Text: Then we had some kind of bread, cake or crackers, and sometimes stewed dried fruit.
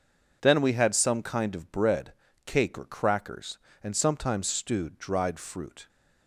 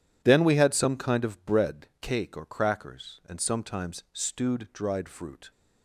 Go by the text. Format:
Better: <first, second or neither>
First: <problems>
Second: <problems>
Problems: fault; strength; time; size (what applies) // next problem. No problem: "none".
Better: neither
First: none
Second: none